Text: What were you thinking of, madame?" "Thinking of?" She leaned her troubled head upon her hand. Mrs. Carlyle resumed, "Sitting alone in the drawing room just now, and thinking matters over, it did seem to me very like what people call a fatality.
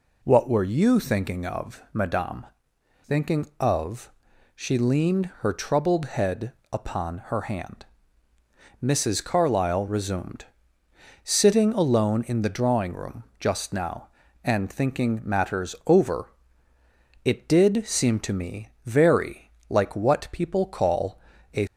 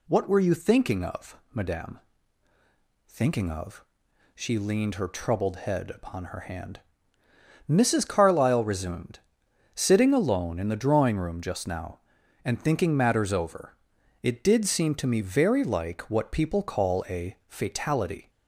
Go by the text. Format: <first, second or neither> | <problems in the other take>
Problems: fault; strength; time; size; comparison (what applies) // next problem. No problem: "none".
second | pauses between "head" and "upon"; slight; at 6.5 s; 0.22 s long // pauses between "room" and "just"; slight; at 13.2 s; 0.16 s long // pauses between "me" and "very"; slight; at 18.6 s; 0.16 s long // pauses between "very" and "like"; slight; at 19.4 s; 0.20 s long // pauses between "call" and "a"; slight; at 21.1 s; 0.36 s long // stops before "fatality"; at 21.6 s